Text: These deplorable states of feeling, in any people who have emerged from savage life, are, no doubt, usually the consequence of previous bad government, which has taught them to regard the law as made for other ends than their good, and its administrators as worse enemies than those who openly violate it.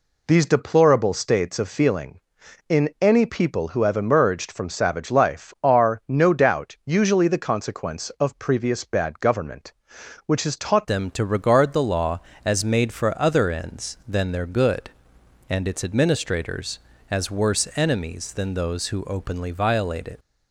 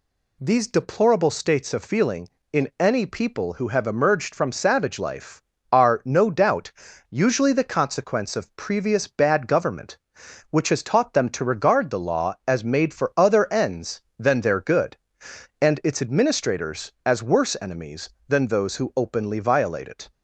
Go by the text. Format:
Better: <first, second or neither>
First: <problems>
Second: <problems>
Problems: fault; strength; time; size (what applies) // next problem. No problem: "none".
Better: second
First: changes voice at "them"; from 10.8 s on; 9.3 s long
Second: none